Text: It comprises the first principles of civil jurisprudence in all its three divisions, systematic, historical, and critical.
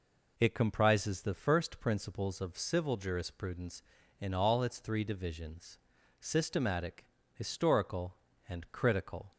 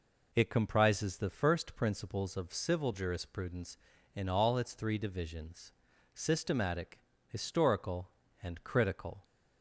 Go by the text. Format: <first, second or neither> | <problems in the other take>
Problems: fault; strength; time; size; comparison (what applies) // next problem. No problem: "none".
neither | none